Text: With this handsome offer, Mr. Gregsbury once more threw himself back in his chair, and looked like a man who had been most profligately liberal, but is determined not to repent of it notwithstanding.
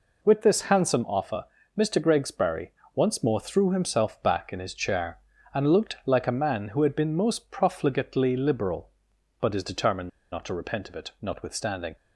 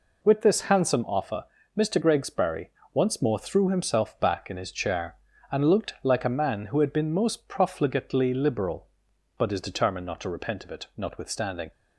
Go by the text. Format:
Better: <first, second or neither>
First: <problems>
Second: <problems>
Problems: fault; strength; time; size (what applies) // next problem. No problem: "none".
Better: second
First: pauses between "Gregsbury" and "once"; slight; at 2.6 s; 0.24 s long // pauses between "determined" and "not"; slight; at 10.0 s; 0.24 s long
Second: pauses between "Gregsbury" and "once"; slight; at 2.6 s; 0.24 s long